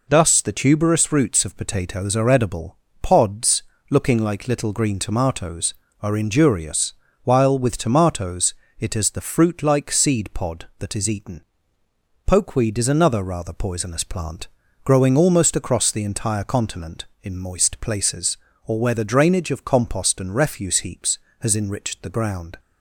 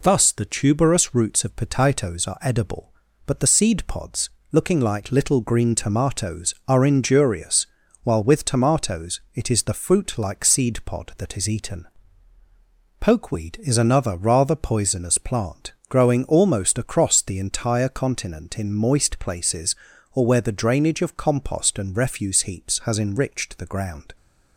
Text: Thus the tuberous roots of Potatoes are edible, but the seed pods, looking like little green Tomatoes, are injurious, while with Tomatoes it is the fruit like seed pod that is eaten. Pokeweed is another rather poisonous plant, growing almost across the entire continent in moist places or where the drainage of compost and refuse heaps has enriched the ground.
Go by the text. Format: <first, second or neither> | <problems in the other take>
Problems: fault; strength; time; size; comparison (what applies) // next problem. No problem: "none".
second | skips "but the seed"; at 2.8 s // pauses between "Tomatoes" and "it"; slight; at 8.5 s; 0.26 s long